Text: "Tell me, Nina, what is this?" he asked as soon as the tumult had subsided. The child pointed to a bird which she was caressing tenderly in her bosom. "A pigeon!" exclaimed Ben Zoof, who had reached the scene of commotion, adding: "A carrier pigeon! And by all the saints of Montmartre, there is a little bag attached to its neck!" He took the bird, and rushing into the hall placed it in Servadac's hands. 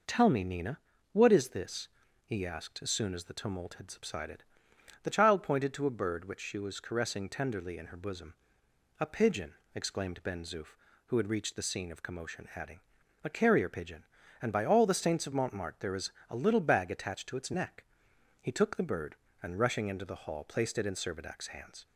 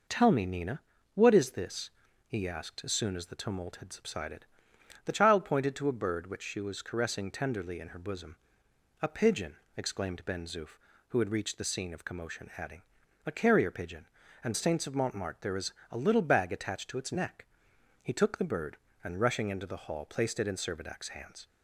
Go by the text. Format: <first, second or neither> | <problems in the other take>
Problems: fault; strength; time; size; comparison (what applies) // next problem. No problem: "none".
first | skips "by all the"; at 14.5 s // pauses between "is" and "a"; slight; at 15.7 s; 0.16 s long; slight in the first